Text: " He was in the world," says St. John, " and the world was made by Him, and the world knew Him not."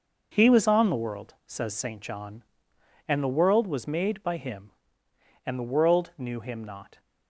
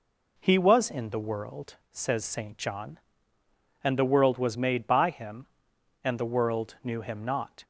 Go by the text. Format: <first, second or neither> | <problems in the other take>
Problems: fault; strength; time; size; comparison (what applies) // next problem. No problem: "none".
second | says "on" for "in"; at 0.6 s